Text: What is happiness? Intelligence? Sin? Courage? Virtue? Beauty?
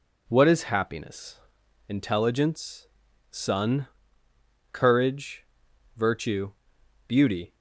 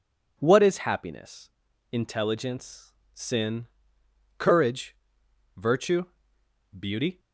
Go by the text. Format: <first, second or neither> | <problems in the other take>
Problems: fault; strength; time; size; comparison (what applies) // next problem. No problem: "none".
second | says "Sun" for "Sin"; at 3.3 s